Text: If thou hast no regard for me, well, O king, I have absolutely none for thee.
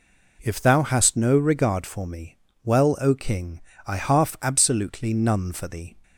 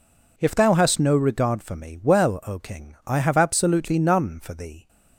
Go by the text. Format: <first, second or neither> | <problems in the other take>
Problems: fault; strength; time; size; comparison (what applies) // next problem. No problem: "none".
second | says "half" for "have"; at 3.9 s